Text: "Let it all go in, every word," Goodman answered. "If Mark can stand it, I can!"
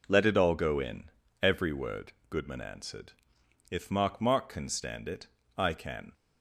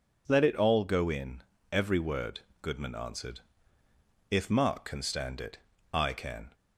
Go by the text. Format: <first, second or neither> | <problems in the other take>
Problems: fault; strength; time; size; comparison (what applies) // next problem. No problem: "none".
second | says "Mark" twice; at 4.2 s